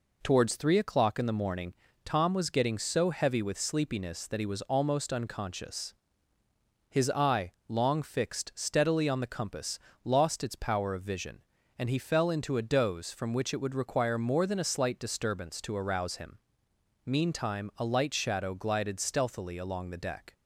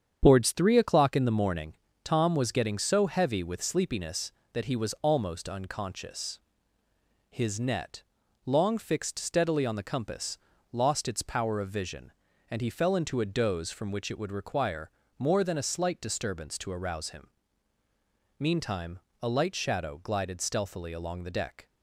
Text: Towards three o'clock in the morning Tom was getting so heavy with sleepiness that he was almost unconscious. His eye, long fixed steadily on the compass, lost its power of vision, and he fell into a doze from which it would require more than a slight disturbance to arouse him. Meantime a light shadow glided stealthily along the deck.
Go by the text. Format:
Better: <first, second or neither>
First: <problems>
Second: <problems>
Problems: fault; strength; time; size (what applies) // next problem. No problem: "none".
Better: first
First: pauses between "morning" and "Tom"; slight; at 1.7 s; 0.30 s long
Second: starts louder than the rest; strong; until 1.2 s; 8 dB // pauses between "morning" and "Tom"; slight; at 1.7 s; 0.28 s long // says "net" for "eye"; at 7.5 s // pauses between "require" and "more"; slight; at 14.8 s; 0.28 s long // pauses between "Meantime" and "a"; slight; at 18.9 s; 0.22 s long